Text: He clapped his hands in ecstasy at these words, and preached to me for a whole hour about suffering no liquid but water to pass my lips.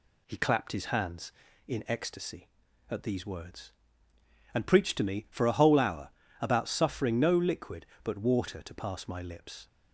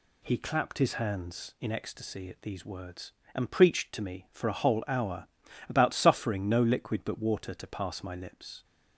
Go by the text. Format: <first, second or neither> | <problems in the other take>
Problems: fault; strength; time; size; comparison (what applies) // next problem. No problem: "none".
neither | pauses between "hour" and "about"; the same in both